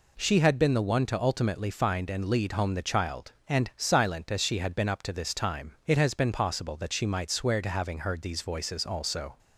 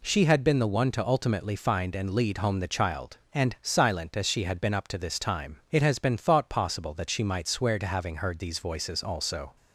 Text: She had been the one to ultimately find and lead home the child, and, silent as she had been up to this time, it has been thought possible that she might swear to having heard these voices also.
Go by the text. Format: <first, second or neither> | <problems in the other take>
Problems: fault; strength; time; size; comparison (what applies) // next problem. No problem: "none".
second | skips "thought"; at 6.3 s